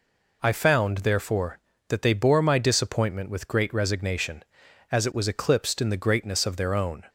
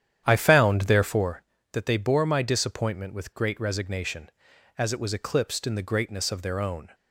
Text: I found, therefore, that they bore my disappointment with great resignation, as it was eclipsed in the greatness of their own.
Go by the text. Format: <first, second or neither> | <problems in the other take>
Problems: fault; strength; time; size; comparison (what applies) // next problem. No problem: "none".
first | starts louder than the rest; strong; until 1.4 s; 10 dB